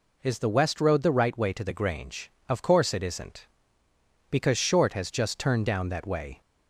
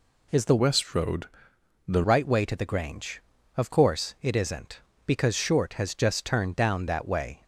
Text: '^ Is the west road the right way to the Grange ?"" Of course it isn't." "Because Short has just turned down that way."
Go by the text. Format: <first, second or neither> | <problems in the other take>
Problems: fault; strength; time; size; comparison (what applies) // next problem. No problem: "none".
first | changes voice from "west" to "the"; from 0.5 to 2.0 s; 1.5 s long // pauses between "road" and "the"; noticeable; at 1.2 s; 0.62 s long